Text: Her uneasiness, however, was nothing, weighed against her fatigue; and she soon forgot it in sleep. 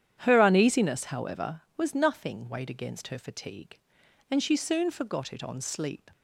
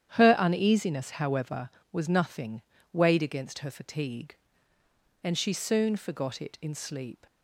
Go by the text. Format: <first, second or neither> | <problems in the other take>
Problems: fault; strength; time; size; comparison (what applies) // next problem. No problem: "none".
second | starts louder than the rest; strong; until 1.2 s; 10 dB; strong in the second // says "on" for "in"; at 5.4 s